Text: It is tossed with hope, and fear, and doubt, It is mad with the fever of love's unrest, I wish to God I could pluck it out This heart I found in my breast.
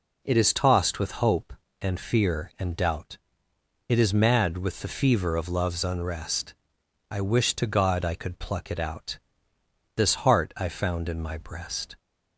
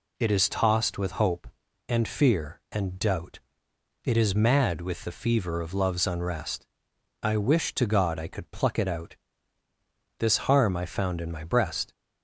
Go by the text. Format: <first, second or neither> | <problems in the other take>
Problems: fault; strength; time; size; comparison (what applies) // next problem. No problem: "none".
first | pauses between "out" and "This"; at 9.1 s; 1.0 s long; noticeable in the first // says "harm" for "heart"; at 10.3 s